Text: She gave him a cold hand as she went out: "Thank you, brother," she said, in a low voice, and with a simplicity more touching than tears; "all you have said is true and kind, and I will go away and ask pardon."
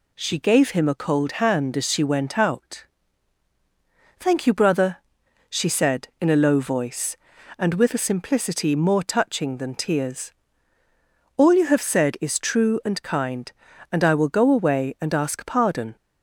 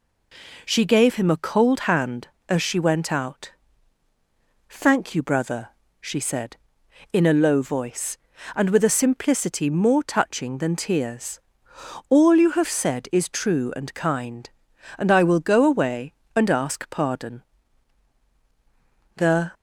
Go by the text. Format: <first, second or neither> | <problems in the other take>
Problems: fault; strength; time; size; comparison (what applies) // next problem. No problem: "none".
first | goes on to say "The"; slight; from 19.1 s on; 0.36 s long